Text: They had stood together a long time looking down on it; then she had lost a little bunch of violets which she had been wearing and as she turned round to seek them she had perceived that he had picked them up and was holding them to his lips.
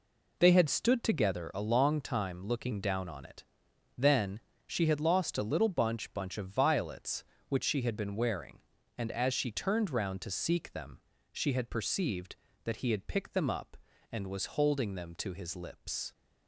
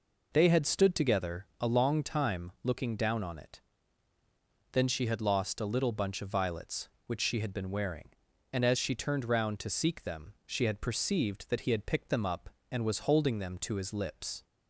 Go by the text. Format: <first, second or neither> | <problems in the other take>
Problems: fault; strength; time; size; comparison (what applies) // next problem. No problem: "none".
second | pauses between "then" and "she"; slight; at 4.3 s; 0.28 s long // says "bunch" twice; at 6.1 s // pauses between "them" and "she"; slight; at 10.9 s; 0.34 s long